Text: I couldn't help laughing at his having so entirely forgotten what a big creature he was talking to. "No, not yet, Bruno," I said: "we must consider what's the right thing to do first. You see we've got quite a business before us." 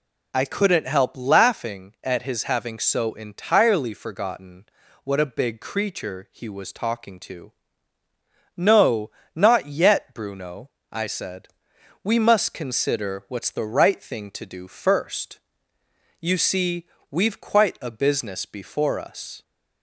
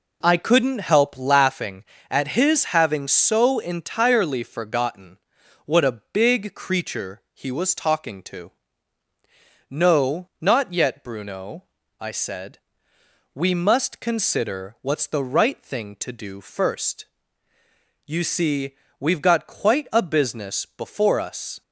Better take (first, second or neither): second